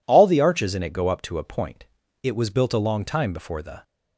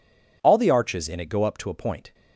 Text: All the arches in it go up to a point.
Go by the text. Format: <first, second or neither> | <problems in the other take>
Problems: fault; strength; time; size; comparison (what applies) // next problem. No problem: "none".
second | goes on to say "It was built a long time before the"; from 2.2 s on; 1.6 s long